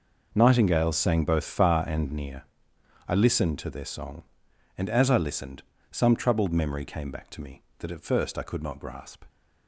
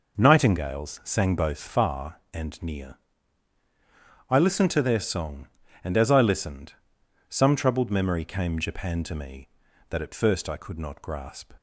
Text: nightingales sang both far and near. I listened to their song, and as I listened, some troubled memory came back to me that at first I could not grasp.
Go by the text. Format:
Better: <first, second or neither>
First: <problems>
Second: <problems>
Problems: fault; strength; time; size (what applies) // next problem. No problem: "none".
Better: first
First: none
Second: says "japan" for "back"; at 8.5 s